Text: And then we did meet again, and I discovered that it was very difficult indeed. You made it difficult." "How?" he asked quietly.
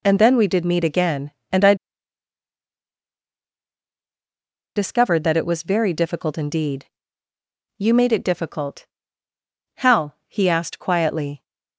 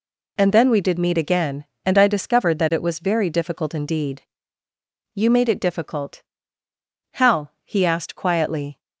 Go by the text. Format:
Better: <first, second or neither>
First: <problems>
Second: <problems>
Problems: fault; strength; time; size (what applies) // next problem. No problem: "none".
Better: second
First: pauses between "I" and "discovered"; strong; at 1.7 s; 3.0 s long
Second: none